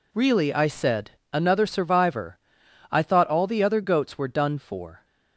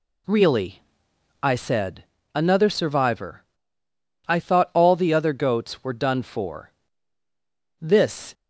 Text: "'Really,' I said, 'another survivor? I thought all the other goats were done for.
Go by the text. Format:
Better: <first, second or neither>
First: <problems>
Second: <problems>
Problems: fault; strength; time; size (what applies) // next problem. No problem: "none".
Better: first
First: none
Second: goes on to say "This"; from 7.8 s on; 0.52 s long